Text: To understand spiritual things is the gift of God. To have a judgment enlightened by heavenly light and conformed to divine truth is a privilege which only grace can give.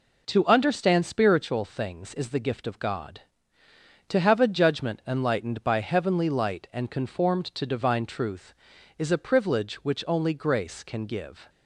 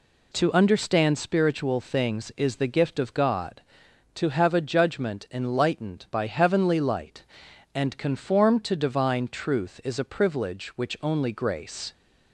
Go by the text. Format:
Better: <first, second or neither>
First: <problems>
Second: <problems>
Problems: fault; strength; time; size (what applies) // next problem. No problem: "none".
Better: first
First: none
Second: stops before "can give"; at 11.9 s